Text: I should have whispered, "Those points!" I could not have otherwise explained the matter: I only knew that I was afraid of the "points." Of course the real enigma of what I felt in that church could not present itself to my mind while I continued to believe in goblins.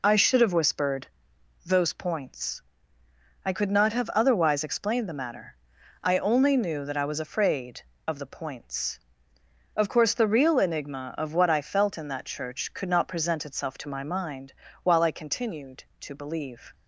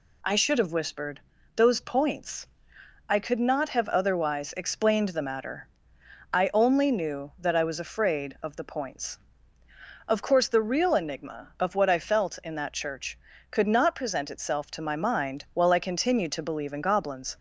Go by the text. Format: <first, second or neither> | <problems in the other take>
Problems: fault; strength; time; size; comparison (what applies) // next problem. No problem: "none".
second | pauses between "mind" and "while"; slight; at 14.5 s; 0.32 s long // stops before "in goblins"; at 16.7 s